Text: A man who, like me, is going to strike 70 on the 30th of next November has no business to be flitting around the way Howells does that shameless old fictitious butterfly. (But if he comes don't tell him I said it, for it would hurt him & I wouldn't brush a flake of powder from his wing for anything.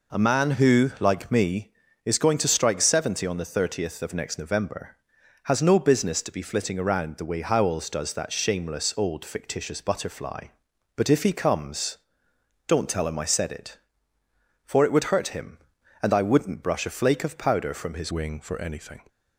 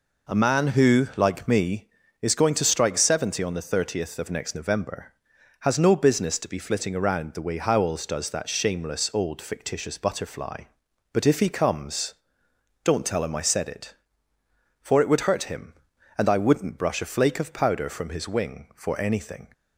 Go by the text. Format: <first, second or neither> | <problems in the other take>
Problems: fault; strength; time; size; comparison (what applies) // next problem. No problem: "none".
second | pauses between "comes" and "don't"; noticeable; at 11.9 s; 0.68 s long; noticeable in the second // changes voice at "wing"; from 18.0 s on; 1.0 s long